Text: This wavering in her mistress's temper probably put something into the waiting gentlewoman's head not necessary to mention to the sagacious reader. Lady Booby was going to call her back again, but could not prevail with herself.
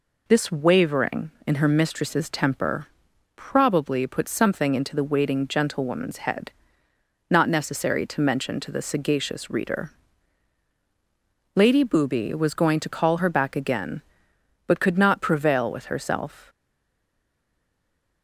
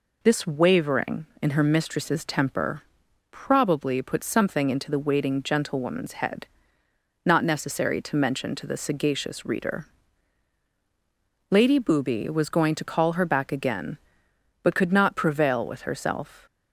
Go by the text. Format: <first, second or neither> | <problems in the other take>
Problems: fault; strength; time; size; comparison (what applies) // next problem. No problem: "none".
second | pauses between "temper" and "probably"; noticeable; at 2.8 s; 0.48 s long; noticeable in the second // pauses between "head" and "not"; noticeable; at 6.5 s; 0.76 s long; noticeable in the second // stays silent after the last word; noticeable; from 16.4 s on; 1.8 s long